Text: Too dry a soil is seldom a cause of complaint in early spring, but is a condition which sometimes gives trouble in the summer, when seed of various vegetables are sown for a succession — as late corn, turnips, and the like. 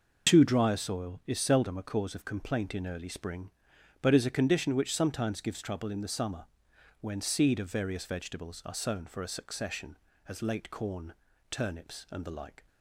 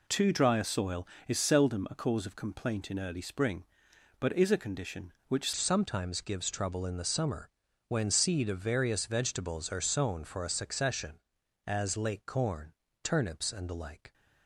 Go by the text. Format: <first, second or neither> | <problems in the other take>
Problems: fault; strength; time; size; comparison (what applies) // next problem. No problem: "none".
first | changes voice at "sometimes"; from 5.5 s on; 8.6 s long